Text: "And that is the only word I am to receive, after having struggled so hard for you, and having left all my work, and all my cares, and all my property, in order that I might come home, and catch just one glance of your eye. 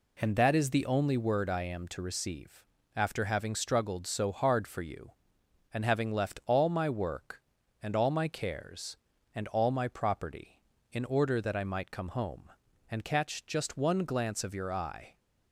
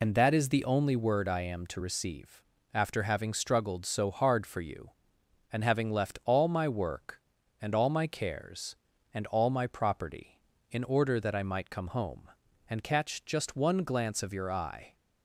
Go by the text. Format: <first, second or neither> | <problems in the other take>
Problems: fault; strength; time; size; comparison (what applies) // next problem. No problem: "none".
first | loses the start of "And"; at 0.0 s; 50 ms